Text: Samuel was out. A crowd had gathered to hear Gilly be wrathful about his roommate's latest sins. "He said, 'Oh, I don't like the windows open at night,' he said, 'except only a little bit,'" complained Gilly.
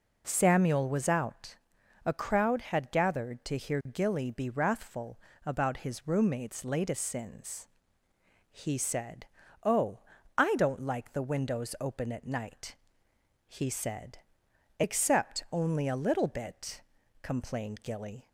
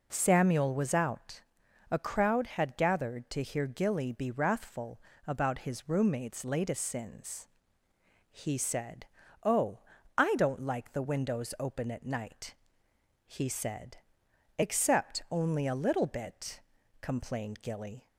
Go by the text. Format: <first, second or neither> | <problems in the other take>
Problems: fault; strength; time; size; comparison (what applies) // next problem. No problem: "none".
neither | pauses between "wrathful" and "about"; slight; the same in both